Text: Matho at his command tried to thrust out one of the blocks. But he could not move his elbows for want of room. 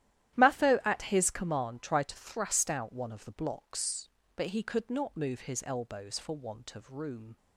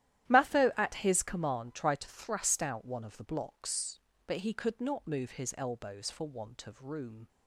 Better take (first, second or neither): neither